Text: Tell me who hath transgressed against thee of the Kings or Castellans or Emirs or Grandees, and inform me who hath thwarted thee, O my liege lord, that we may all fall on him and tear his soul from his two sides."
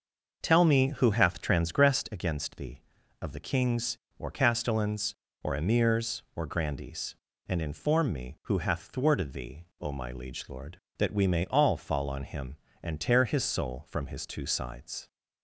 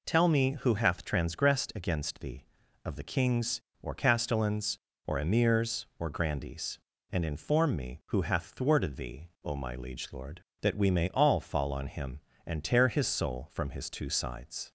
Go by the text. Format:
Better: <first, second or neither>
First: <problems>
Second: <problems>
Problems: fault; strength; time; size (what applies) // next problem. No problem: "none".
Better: second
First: starts louder than the rest; until 2.2 s; 6 dB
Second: none